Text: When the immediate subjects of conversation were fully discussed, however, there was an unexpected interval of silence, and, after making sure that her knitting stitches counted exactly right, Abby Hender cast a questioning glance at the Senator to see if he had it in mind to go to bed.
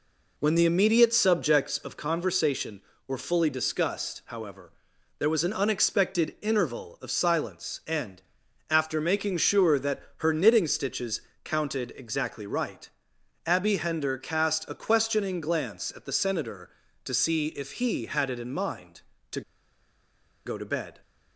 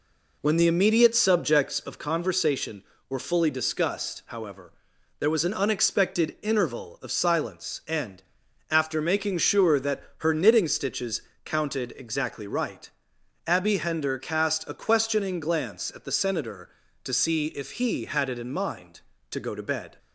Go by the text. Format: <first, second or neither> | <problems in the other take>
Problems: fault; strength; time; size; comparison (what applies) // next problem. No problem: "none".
second | pauses between "stitches" and "counted"; slight; at 11.2 s; 0.24 s long; slight in the second // pauses between "to" and "go"; at 19.4 s; 1.0 s long